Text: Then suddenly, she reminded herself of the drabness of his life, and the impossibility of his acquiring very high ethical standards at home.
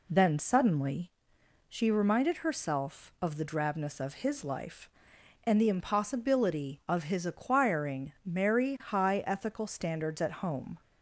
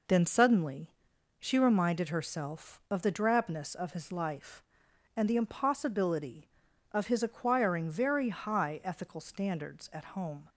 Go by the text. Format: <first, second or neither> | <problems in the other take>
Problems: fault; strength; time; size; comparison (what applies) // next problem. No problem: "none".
second | says "merry" for "very"; at 8.2 s